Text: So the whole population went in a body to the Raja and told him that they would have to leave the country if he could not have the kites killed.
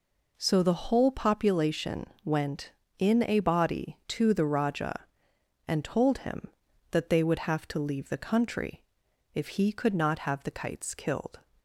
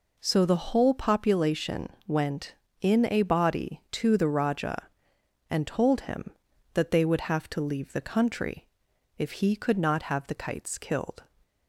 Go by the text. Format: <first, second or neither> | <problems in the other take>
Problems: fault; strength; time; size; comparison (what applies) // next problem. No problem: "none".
neither | pauses between "population" and "went"; slight; the same in both // pauses between "country" and "if"; noticeable; the same in both